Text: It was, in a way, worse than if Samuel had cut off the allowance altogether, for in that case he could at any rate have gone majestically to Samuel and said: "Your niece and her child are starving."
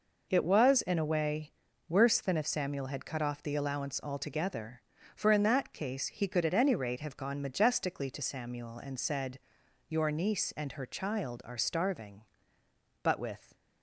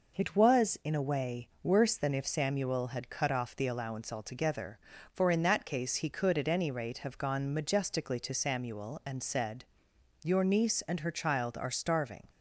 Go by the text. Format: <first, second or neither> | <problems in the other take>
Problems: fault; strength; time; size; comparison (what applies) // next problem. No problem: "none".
second | goes on to say "But with"; from 13.0 s on; 0.52 s long